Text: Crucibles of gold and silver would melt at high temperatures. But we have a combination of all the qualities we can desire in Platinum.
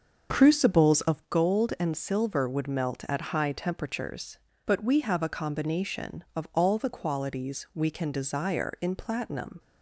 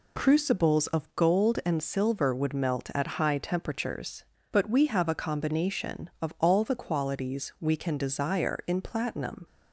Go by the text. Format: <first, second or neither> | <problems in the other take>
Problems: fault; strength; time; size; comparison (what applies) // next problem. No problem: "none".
second | starts louder than the rest; until 1.2 s; 6 dB